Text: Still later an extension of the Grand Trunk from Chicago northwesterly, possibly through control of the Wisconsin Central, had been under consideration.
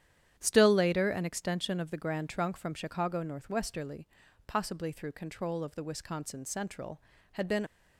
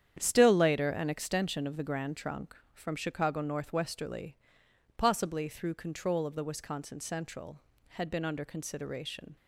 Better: second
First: starts louder than the rest; strong; until 1.3 s; 10 dB // stops before "under consideration"; at 7.6 s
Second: starts louder than the rest; strong; until 1.2 s; 9 dB

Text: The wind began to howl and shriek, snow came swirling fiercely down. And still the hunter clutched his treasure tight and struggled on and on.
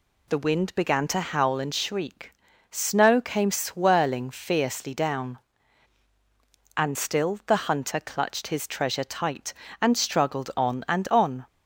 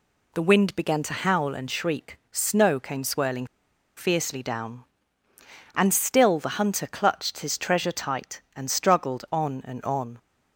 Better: first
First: none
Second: pauses between "swirling" and "fiercely"; noticeable; at 3.4 s; 0.52 s long

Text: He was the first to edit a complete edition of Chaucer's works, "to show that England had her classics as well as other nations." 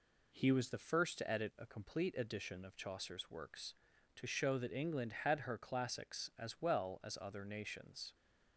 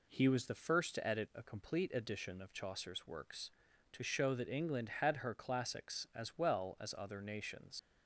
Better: first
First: none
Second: leaves "nations" unfinished; at 7.7 s; 120 ms

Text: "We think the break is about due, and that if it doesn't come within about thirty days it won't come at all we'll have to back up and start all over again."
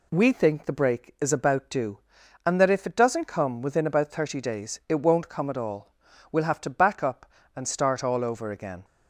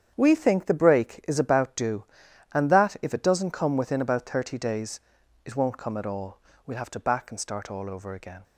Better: first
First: pauses between "all" and "we'll"; at 5.9 s; 0.40 s long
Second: starts louder than the rest; strong; until 1.1 s; 8.5 dB // pauses between "days" and "it"; at 4.9 s; 0.44 s long // pauses between "all" and "we'll"; slight; at 6.3 s; 0.30 s long // skips "up"; at 7.3 s

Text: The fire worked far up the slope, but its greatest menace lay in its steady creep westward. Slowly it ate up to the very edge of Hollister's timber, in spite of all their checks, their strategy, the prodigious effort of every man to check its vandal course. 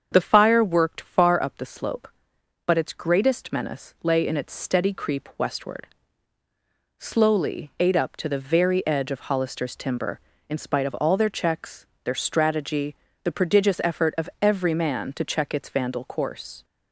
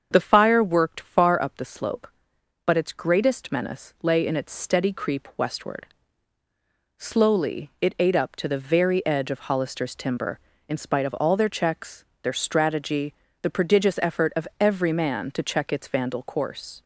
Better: second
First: starts louder than the rest; strong; until 1.1 s; 7 dB // skips "it"; at 7.7 s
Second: starts louder than the rest; strong; until 1.1 s; 7 dB

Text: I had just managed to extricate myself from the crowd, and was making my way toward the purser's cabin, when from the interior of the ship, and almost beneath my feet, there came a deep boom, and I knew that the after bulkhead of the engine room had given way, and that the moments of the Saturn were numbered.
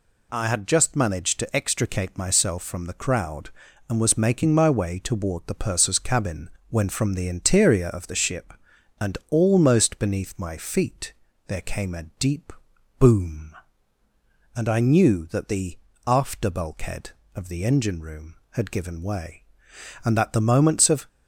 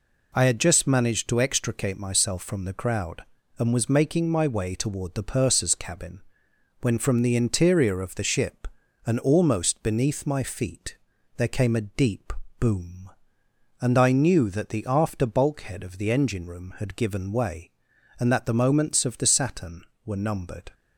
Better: second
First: pauses between "a" and "deep"; slight; at 12.0 s; 0.16 s long // pauses between "deep" and "boom"; noticeable; at 12.5 s; 0.48 s long // pauses between "the" and "after"; slight; at 15.7 s; 0.28 s long // stops before "the Saturn were numbered"; at 21.0 s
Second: pauses between "deep" and "boom"; slight; at 12.3 s; 0.26 s long

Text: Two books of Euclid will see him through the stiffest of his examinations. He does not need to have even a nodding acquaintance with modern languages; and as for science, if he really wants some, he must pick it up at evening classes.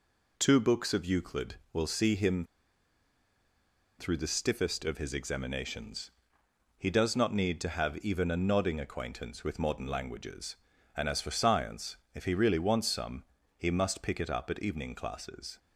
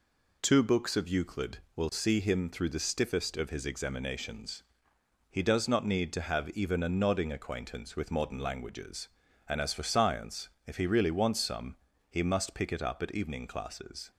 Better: second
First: pauses between "him" and "through"; strong; at 2.4 s; 1.5 s long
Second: none

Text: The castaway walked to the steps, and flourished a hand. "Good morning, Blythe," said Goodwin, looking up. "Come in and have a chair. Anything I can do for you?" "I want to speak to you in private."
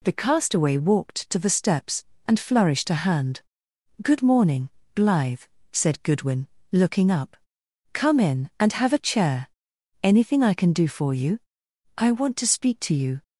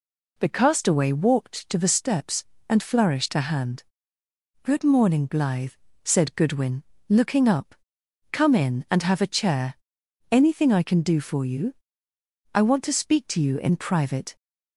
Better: second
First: stops before "in private"; at 13.2 s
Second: none

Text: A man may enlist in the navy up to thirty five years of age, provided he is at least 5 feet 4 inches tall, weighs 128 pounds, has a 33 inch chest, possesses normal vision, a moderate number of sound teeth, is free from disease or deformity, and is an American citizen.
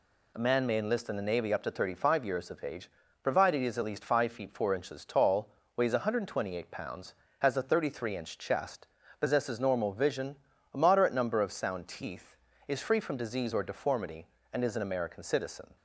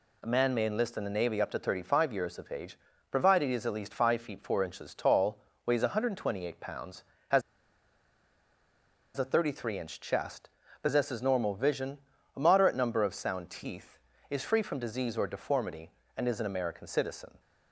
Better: first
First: none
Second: pauses between "has" and "a"; strong; at 7.4 s; 1.7 s long

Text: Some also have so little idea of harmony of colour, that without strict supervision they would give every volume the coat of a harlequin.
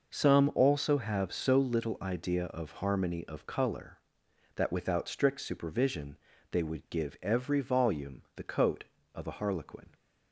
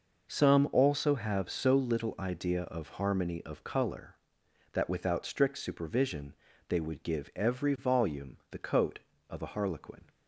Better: neither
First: pauses between "supervision" and "they"; slight; at 6.1 s; 0.34 s long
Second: pauses between "supervision" and "they"; slight; at 6.3 s; 0.34 s long

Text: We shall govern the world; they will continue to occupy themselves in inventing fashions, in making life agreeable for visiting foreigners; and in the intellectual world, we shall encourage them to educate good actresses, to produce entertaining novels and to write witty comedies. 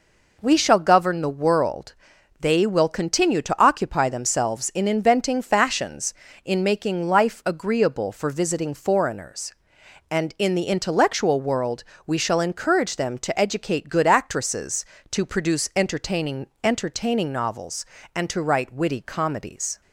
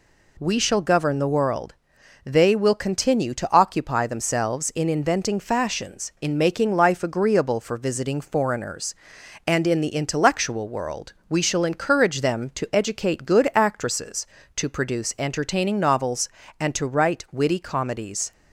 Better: second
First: says "entertaining" twice; at 16.6 s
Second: none

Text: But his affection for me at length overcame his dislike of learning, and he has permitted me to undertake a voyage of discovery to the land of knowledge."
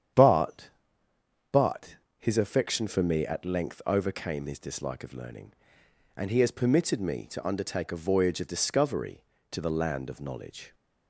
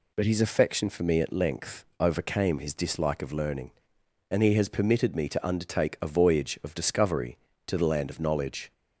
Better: second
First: starts louder than the rest; strong; until 1.9 s; 9 dB // says "But" twice; at 1.5 s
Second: none

